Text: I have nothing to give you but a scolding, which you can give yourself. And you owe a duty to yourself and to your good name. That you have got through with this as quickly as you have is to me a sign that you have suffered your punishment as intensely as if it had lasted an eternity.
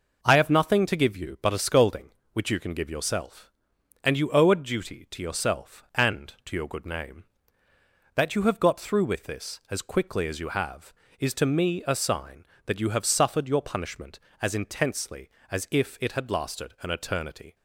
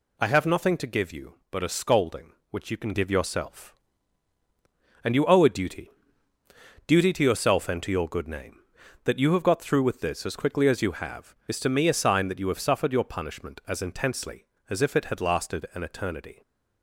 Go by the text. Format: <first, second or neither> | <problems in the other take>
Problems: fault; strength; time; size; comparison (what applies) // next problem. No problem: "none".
first | says "duty" twice; at 6.8 s